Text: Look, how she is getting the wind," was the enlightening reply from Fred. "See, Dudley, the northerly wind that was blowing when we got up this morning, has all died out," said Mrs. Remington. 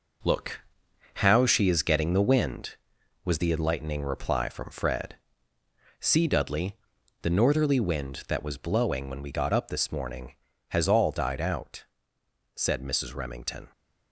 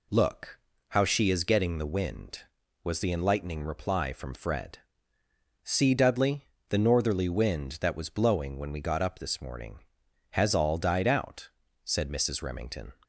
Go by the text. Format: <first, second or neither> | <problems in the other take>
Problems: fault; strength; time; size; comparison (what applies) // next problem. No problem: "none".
second | gets quieter; strong; throughout; 7 dB